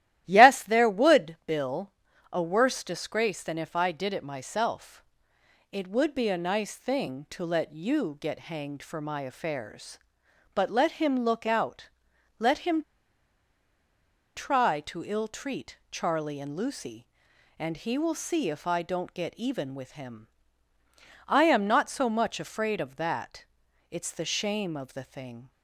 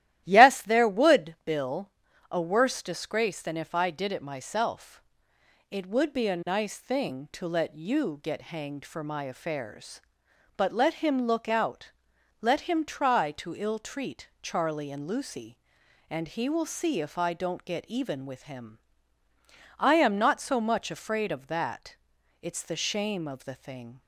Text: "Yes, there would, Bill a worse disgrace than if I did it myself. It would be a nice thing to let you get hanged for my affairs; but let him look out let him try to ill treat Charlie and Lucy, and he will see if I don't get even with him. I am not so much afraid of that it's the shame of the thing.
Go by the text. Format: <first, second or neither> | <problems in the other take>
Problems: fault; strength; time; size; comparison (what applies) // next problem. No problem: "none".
second | starts louder than the rest; strong; until 1.2 s; 13.5 dB; strong in the second // pauses between "Bill" and "a"; at 1.9 s; 0.42 s long; also in the second // pauses between "out" and "let"; noticeable; at 11.9 s; 0.48 s long; noticeable in the second // pauses between "him" and "try"; strong; at 12.8 s; 1.5 s long // pauses between "that" and "it's"; noticeable; at 23.4 s; 0.48 s long; noticeable in the second